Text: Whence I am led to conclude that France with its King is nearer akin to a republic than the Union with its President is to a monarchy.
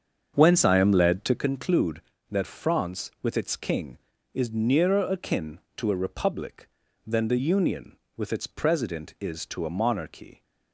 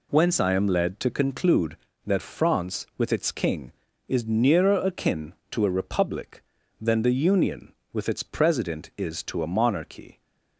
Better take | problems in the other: second | starts louder than the rest; until 1.4 s; 7 dB

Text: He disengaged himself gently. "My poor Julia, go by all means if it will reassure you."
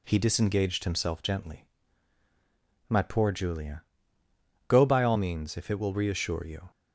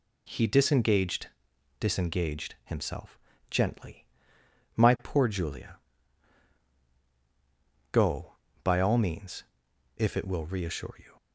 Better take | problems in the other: first | says "disengaged" twice; at 1.7 s // pauses between "himself" and "gently"; slight; at 3.1 s; 0.32 s long // pauses between "means" and "if"; noticeable; at 9.4 s; 0.54 s long

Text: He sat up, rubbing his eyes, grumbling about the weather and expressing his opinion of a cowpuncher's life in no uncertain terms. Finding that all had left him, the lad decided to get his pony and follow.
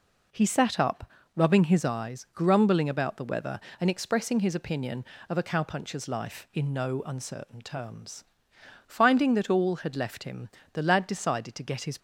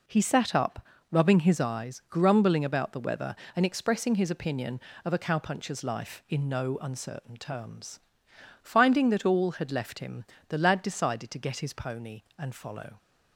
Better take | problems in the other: second | stops before "pony and follow"; at 11.9 s

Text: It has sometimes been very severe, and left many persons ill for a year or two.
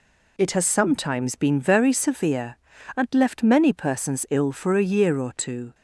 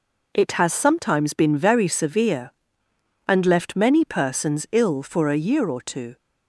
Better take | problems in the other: neither | none

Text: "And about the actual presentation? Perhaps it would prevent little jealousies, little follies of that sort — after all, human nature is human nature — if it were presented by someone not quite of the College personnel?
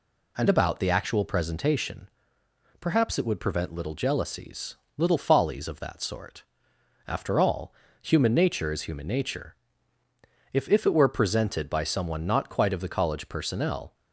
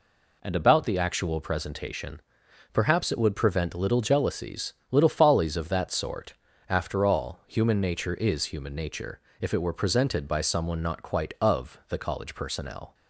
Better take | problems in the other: second | says "if" twice; at 10.6 s

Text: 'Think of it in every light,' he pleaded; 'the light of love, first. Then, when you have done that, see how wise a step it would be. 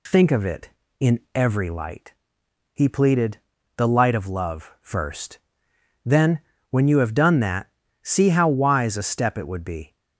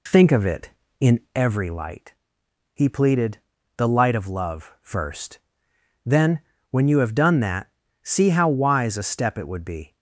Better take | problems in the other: first | starts louder than the rest; slight; until 1.5 s; 2 dB // pauses between "in" and "every"; slight; at 1.1 s; 0.16 s long; slight in the first

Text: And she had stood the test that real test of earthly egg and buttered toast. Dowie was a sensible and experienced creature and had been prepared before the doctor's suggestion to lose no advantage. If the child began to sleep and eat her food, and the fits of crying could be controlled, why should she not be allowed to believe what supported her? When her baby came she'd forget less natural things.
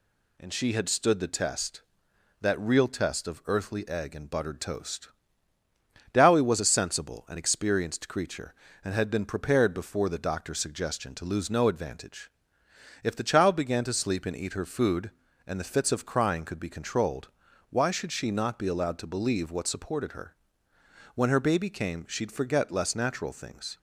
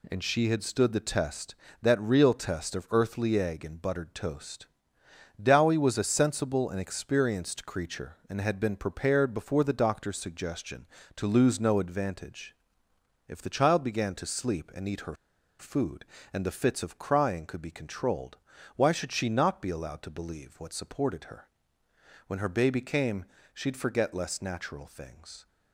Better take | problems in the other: first | pauses between "her" and "food"; at 15.1 s; 0.44 s long // pauses between "came" and "she'd"; slight; at 23.2 s; 0.28 s long

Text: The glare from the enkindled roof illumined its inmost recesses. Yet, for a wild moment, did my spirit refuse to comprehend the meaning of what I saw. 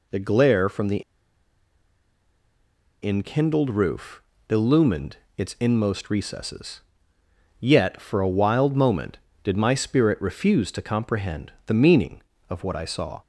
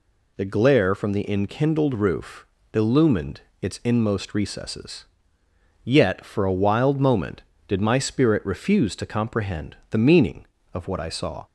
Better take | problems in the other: second | pauses between "the" and "enkindled"; strong; at 1.0 s; 2.0 s long // pauses between "roof" and "illumined"; slight; at 4.2 s; 0.26 s long; slight in the second // pauses between "illumined" and "its"; slight; at 5.1 s; 0.22 s long; slight in the second

